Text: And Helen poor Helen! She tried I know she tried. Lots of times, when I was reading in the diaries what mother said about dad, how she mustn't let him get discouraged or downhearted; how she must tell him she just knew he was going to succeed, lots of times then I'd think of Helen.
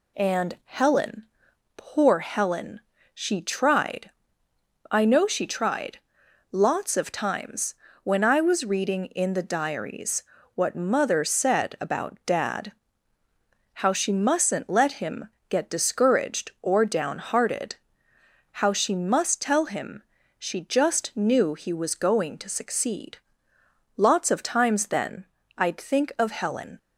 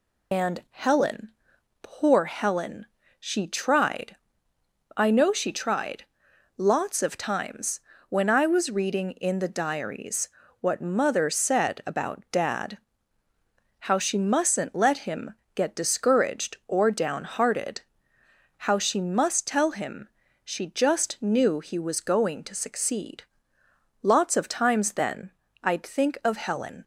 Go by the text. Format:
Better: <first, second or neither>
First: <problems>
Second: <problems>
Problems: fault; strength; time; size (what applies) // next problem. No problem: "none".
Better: first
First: pauses between "Helen" and "poor"; noticeable; at 1.2 s; 0.52 s long // pauses between "tried" and "I"; noticeable; at 4.0 s; 0.80 s long // pauses between "diaries" and "what"; slight; at 10.2 s; 0.30 s long // pauses between "him" and "get"; slight; at 15.2 s; 0.20 s long // pauses between "him" and "she"; slight; at 20.0 s; 0.34 s long // pauses between "then" and "I'd"; slight; at 25.2 s; 0.32 s long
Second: loses the start of "And"; at 0.3 s; 100 ms // pauses between "Helen" and "poor"; noticeable; at 1.2 s; 0.52 s long // pauses between "tried" and "I"; noticeable; at 4.1 s; 0.80 s long // pauses between "diaries" and "what"; slight; at 10.2 s; 0.30 s long // pauses between "him" and "get"; slight; at 15.3 s; 0.20 s long // pauses between "him" and "she"; slight; at 20.0 s; 0.34 s long // pauses between "then" and "I'd"; slight; at 25.3 s; 0.32 s long